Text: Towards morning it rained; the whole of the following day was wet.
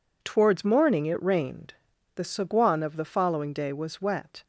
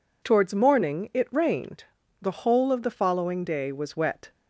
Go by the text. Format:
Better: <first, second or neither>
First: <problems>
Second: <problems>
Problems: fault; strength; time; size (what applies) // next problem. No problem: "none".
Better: second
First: says "saguan" for "whole"; at 2.2 s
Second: none